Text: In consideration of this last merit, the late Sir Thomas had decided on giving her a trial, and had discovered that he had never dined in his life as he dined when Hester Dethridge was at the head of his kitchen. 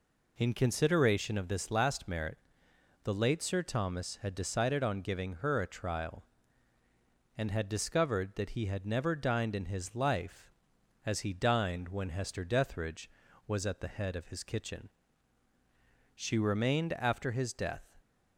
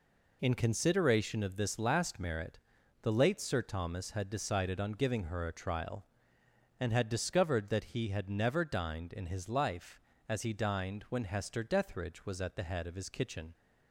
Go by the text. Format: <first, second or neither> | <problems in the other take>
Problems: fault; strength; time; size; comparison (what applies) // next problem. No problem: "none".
second | goes on to say "She remained after his death"; strong; from 16.1 s on; 1.7 s long